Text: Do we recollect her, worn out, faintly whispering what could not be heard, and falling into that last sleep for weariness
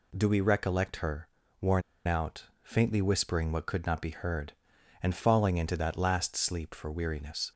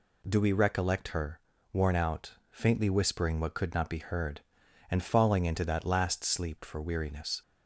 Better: second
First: pauses between "worn" and "out"; slight; at 1.8 s; 0.25 s long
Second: none

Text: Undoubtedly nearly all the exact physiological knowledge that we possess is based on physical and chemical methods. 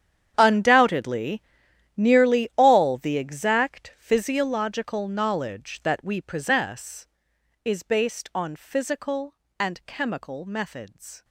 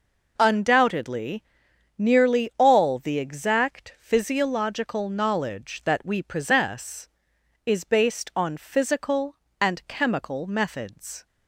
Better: second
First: gets quieter; strong; throughout; 18.5 dB // pauses between "Undoubtedly" and "nearly"; noticeable; at 1.4 s; 0.54 s long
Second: pauses between "Undoubtedly" and "nearly"; noticeable; at 1.4 s; 0.54 s long

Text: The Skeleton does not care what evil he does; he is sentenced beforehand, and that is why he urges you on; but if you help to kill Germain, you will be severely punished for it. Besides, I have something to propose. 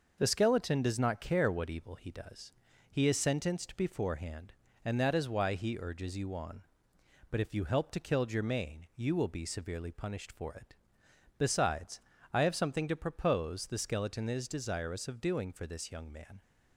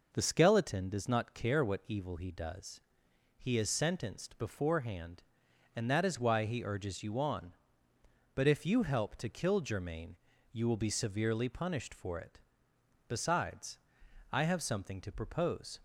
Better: second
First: starts louder than the rest; noticeable; until 1.1 s; 6 dB // goes on to say "The Skeleton is desirous of doing for this young man"; strong; from 13.6 s on; 2.7 s long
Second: none

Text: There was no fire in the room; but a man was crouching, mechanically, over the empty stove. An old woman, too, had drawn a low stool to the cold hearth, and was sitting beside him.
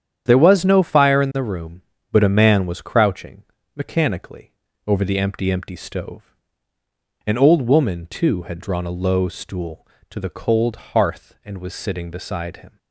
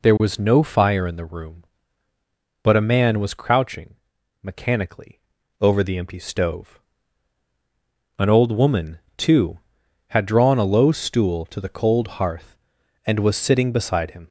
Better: second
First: starts louder than the rest; strong; until 1.2 s; 9 dB // says "empty" twice; at 5.4 s // pauses between "cold" and "hearth"; slight; at 10.7 s; 0.18 s long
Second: none

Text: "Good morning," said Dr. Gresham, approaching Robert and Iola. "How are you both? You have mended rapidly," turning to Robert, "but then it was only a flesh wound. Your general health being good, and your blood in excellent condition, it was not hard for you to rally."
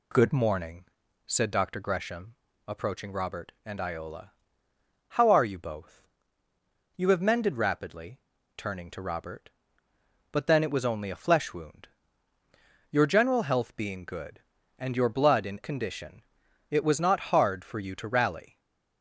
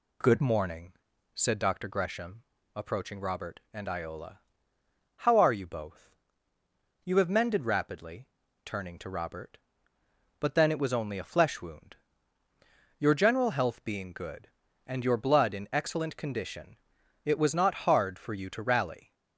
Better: second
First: skips "excellent"; at 15.6 s // stays silent after the last word; slight; from 18.4 s on; 0.6 s long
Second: none

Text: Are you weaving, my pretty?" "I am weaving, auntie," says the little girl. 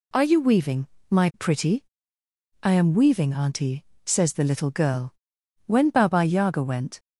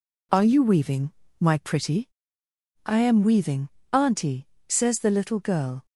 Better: second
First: goes on to say "When Baba Yaga went"; from 5.6 s on; 1.3 s long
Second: none

